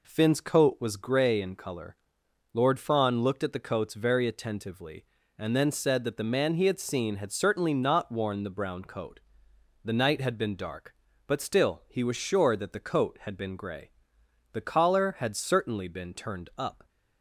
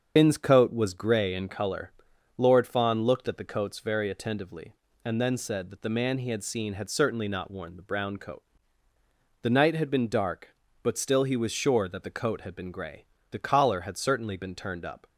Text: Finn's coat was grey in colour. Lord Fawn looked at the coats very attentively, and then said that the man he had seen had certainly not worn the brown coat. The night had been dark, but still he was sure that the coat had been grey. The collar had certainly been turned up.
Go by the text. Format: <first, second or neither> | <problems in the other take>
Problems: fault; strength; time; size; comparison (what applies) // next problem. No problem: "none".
first | loses the start of "Finn's"; at 0.1 s; 85 ms // starts louder than the rest; strong; until 1.1 s; 7 dB